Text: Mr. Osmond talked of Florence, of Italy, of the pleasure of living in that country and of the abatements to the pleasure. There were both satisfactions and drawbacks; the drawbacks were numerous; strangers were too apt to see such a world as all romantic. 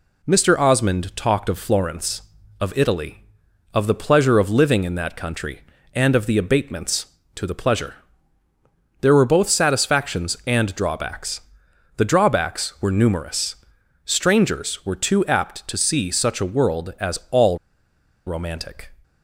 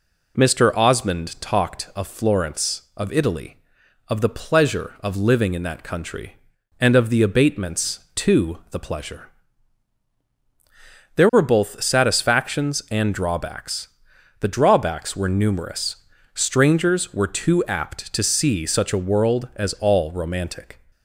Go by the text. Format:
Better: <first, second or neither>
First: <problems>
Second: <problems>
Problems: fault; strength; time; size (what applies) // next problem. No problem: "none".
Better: second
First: pauses between "all" and "romantic"; noticeable; at 17.5 s; 0.68 s long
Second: none